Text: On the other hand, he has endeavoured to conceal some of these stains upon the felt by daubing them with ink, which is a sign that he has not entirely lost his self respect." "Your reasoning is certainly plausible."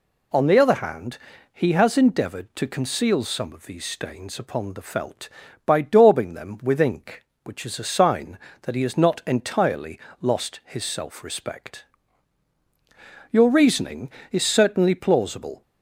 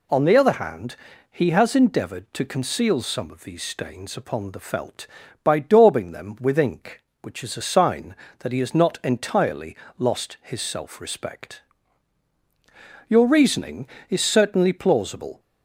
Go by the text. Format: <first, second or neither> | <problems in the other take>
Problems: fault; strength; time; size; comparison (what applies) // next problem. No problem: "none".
neither | pauses between "entirely" and "lost"; slight; the same in both